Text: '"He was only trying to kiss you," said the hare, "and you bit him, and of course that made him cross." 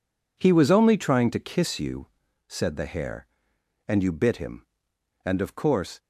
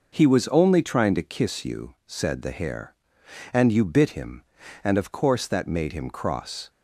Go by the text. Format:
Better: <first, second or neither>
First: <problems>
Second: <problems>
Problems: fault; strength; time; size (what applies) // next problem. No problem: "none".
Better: second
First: stops before "that made him cross"; at 5.9 s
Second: none